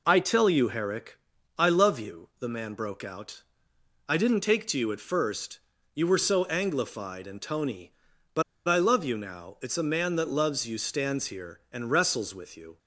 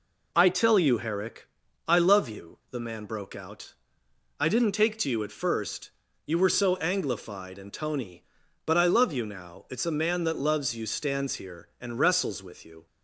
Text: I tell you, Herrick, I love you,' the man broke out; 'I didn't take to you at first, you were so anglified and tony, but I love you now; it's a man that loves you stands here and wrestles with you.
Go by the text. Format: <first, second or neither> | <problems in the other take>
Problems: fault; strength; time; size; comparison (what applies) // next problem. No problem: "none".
second | pauses between "but" and "I"; slight; at 8.4 s; 0.25 s long